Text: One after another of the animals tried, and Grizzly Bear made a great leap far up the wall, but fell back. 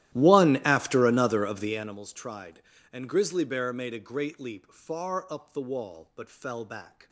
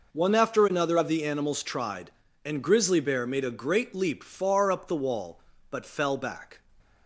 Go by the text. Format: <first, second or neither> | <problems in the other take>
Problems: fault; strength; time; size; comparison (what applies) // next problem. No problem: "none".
second | starts louder than the rest; strong; until 2.0 s; 14 dB